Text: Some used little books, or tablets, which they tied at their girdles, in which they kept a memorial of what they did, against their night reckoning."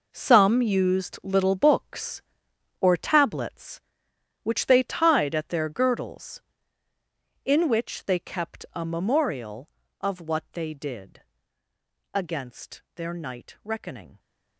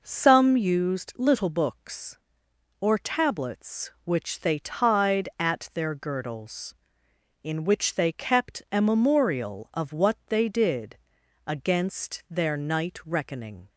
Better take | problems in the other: second | gets quieter; strong; throughout; 12.5 dB

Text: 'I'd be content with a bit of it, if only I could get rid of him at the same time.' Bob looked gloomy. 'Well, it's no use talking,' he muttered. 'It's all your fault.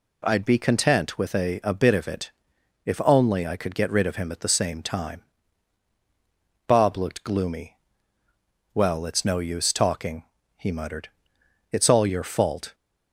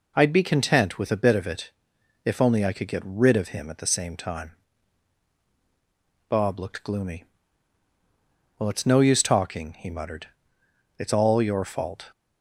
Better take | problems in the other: second | says "a" twice; at 1.6 s

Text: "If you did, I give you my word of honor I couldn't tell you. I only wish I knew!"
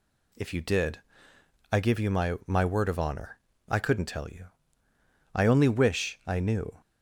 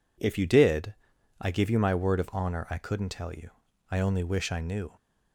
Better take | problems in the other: second | says "my" twice; at 2.4 s // pauses between "honor" and "I"; slight; at 3.3 s; 0.30 s long

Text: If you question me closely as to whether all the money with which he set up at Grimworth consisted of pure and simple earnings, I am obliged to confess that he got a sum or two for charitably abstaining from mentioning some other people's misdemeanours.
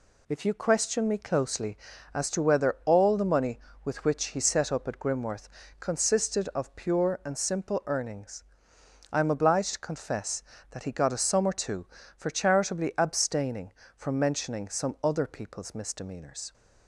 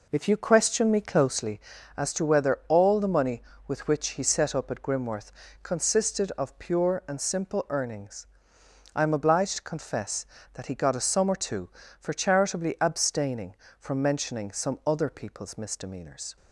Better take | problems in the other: first | starts louder than the rest; noticeable; until 1.4 s; 4 dB // pauses between "Grimworth" and "consisted"; slight; at 5.3 s; 0.30 s long; slight in the first

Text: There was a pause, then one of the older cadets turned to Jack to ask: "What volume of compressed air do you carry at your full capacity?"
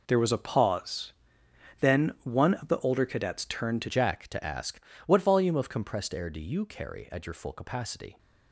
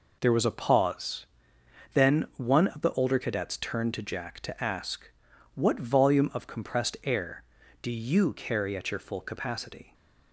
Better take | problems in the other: second | changes voice at "Jack"; from 3.8 s on; 4.3 s long

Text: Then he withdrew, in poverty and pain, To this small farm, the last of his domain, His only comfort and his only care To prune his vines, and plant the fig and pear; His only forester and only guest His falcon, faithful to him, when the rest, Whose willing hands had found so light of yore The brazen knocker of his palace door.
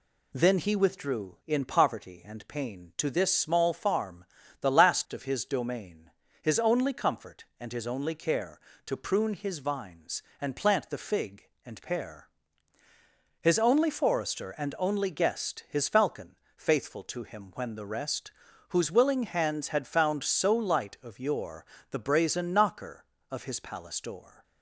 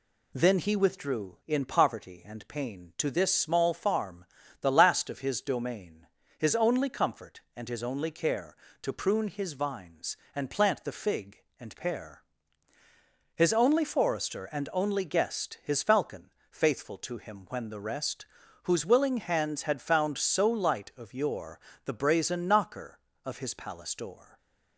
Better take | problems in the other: neither | pauses between "yore" and "The"; slight; the same in both

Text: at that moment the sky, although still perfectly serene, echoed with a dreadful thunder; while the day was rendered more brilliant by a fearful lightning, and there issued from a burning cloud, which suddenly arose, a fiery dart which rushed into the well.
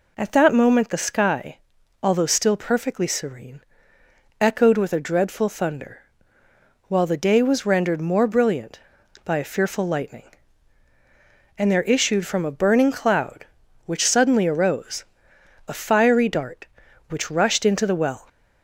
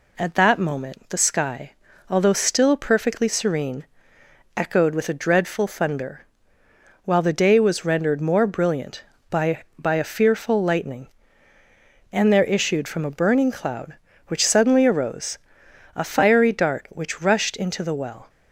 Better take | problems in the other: first | says "by" twice; at 9.7 s

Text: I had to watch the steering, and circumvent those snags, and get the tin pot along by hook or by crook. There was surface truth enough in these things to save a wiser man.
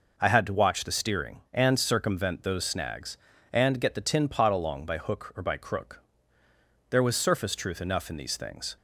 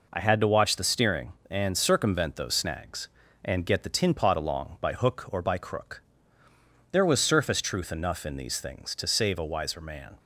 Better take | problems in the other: second | stops before "to save a wiser man"; at 8.7 s

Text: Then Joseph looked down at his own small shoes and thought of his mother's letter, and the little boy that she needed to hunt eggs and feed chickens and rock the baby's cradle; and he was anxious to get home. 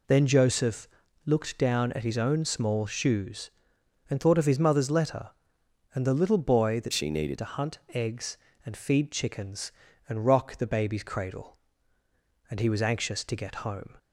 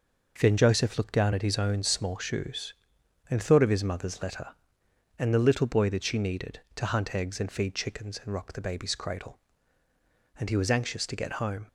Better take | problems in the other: second | pauses between "Joseph" and "looked"; slight; at 0.8 s; 0.36 s long // changes voice from "she" to "needed"; from 6.9 to 7.3 s; 0.4 s long

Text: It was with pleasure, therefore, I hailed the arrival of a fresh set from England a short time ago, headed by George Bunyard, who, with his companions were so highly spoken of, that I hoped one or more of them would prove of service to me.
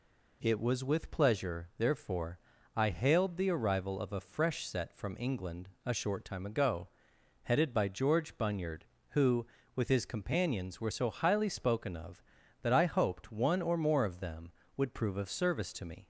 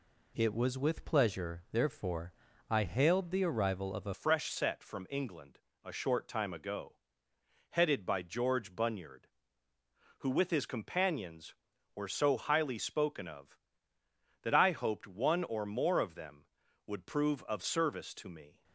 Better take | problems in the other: first | changes voice at "fresh"; from 4.1 s on; 14.5 s long // pauses between "England" and "a"; slight; at 5.5 s; 0.26 s long; slight in the first

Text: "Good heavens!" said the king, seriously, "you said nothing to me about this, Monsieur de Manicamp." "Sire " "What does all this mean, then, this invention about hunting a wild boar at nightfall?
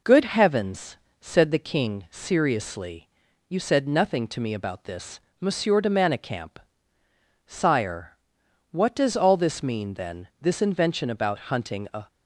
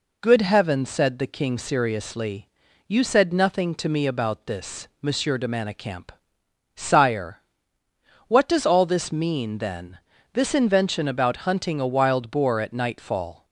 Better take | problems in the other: second | stops before "wild boar at nightfall"; at 12.0 s

